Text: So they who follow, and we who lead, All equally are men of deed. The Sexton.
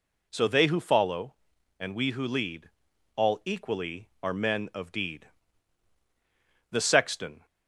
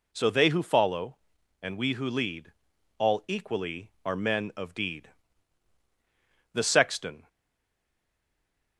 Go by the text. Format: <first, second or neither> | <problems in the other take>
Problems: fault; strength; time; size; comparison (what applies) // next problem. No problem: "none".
first | stays silent after the last word; noticeable; from 7.2 s on; 1.5 s long